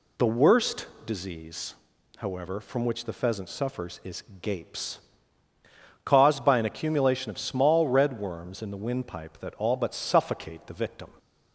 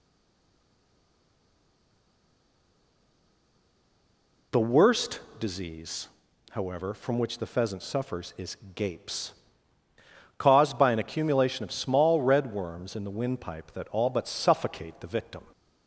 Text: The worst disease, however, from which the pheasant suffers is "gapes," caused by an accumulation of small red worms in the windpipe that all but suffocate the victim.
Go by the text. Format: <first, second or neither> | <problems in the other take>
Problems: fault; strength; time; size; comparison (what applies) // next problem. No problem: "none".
first | stays silent before the first word; strong; until 4.5 s; 4.5 s long // pauses between "worst" and "disease"; slight; at 5.2 s; 0.18 s long; slight in the first // pauses between "is" and "gapes"; slight; at 8.5 s; 0.18 s long; slight in the first